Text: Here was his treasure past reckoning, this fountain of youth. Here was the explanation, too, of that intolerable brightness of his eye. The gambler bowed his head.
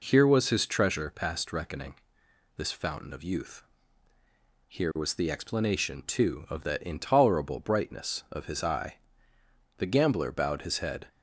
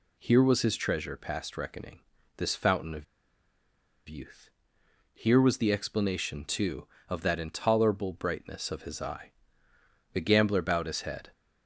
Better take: first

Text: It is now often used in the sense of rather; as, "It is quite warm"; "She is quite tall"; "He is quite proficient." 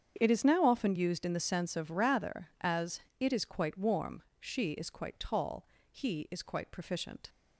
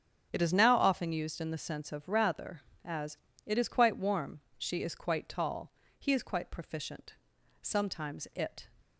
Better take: first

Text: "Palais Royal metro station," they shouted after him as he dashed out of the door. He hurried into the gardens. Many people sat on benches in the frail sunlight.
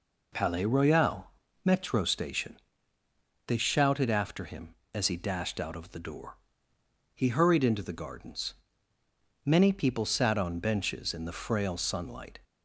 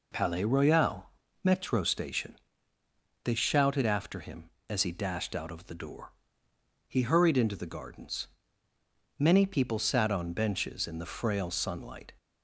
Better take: neither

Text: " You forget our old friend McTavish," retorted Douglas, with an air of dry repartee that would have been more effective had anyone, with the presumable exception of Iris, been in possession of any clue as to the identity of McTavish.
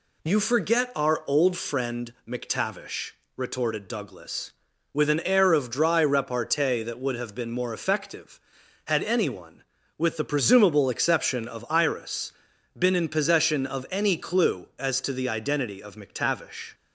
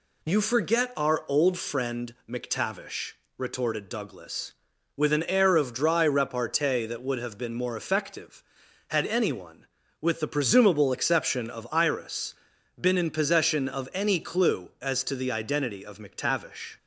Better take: neither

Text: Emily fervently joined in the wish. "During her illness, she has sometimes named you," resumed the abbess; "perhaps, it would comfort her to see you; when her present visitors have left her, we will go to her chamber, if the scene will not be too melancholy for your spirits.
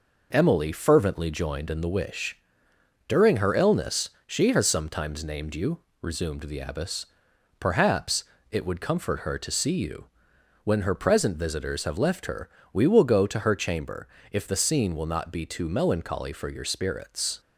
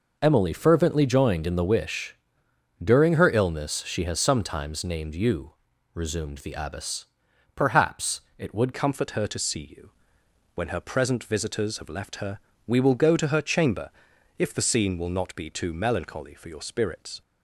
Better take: first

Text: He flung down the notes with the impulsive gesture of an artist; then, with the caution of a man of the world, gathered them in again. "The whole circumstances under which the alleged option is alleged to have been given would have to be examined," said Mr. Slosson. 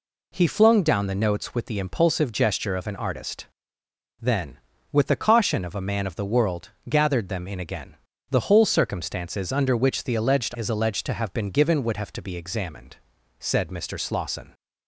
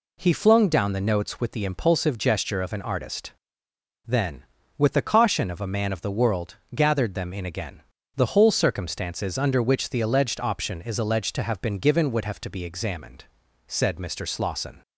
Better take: second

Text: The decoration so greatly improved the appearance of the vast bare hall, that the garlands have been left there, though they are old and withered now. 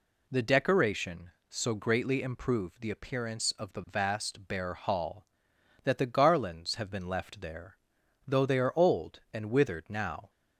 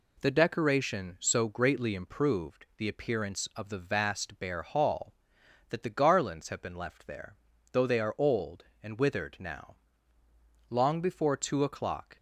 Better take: first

